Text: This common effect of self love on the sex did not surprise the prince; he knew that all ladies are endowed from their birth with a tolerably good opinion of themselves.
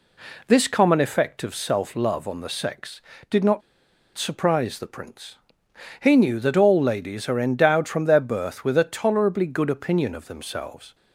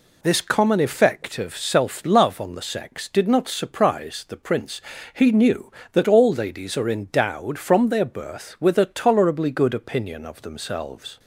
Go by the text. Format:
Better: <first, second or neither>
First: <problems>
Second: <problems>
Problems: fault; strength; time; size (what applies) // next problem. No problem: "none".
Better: second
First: pauses between "not" and "surprise"; noticeable; at 3.6 s; 0.55 s long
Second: none